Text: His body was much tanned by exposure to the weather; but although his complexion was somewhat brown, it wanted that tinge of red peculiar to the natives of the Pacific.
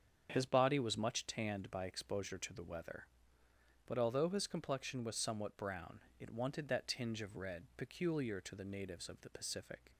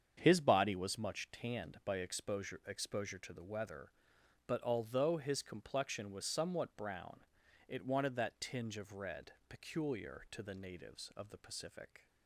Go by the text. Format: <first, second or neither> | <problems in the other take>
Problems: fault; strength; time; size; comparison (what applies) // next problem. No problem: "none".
first | starts louder than the rest; strong; until 1.2 s; 7.5 dB; strong in the first // says "exposure" twice; at 2.6 s // pauses between "red" and "peculiar"; slight; at 9.3 s; 0.18 s long